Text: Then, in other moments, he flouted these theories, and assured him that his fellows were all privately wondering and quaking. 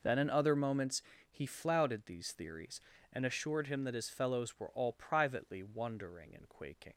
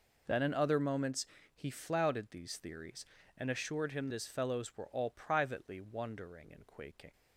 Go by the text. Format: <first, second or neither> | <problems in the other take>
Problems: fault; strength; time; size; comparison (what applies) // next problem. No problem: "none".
first | skips "that"; at 4.0 s